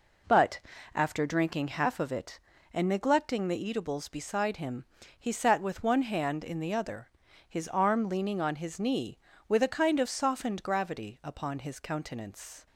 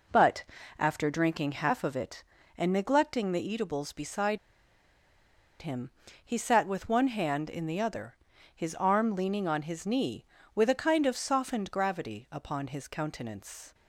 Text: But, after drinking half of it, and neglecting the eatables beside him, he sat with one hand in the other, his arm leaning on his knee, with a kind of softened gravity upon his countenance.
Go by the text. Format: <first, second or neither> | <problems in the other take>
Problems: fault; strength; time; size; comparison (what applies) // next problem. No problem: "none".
first | pauses between "beside" and "him"; at 4.3 s; 1.2 s long